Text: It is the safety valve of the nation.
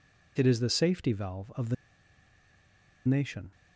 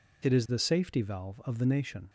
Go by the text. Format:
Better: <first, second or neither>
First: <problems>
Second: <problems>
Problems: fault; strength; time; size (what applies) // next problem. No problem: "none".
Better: second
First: pauses between "the" and "nation"; strong; at 1.7 s; 1.3 s long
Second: none